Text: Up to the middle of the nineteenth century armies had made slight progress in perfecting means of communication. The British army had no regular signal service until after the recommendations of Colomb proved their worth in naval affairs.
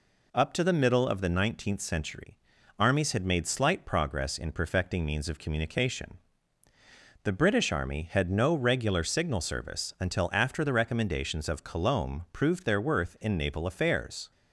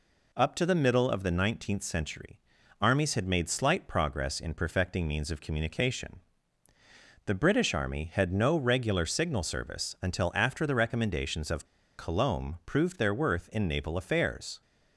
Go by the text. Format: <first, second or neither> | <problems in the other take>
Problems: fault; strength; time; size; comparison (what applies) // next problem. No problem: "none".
first | pauses between "century" and "armies"; at 2.3 s; 0.42 s long; also in the first // pauses between "of" and "Colomb"; slight; at 11.6 s; 0.31 s long